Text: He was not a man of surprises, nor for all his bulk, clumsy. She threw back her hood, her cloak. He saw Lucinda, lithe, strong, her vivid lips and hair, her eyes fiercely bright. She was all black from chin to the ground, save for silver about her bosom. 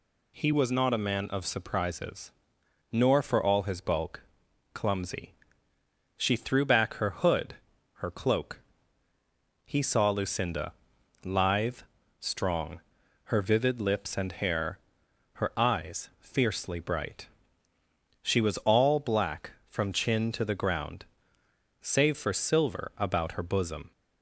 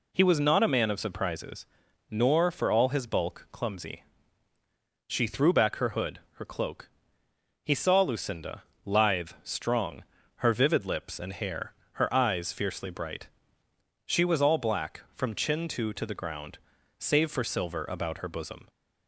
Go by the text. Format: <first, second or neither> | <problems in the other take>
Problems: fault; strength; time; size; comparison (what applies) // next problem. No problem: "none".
first | says "to" twice; at 15.9 s